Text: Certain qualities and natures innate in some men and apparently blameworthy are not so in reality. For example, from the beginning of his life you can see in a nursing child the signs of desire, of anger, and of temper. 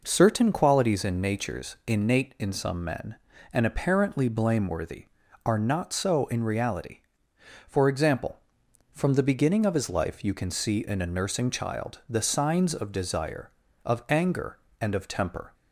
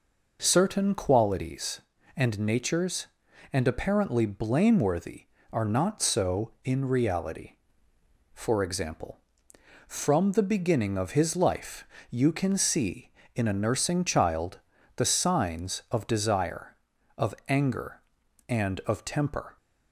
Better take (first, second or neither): first